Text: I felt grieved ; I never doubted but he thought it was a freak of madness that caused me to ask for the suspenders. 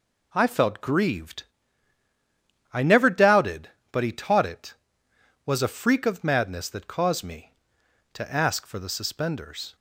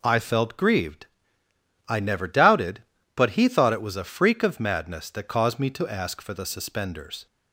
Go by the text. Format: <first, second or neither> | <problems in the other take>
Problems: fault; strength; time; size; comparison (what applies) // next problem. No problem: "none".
second | says "taught" for "thought"; at 4.1 s